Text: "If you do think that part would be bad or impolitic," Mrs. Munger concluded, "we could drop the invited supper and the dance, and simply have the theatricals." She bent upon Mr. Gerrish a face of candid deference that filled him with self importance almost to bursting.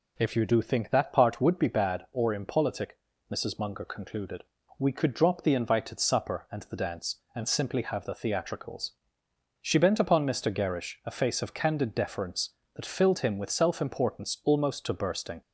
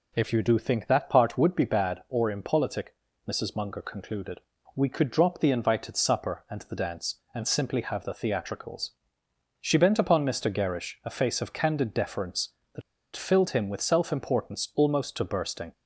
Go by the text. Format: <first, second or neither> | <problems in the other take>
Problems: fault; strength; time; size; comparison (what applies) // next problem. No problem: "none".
first | pauses between "that" and "filled"; slight; at 12.8 s; 0.34 s long